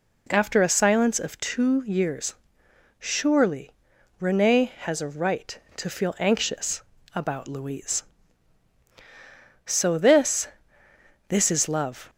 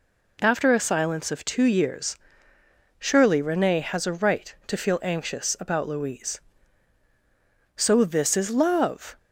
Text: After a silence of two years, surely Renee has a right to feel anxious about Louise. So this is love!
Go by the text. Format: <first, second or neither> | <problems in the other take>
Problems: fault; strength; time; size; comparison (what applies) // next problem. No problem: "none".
second | pauses between "surely" and "Renee"; noticeable; at 3.7 s; 0.48 s long // pauses between "anxious" and "about"; slight; at 6.8 s; 0.34 s long // says "this" twice; at 11.2 s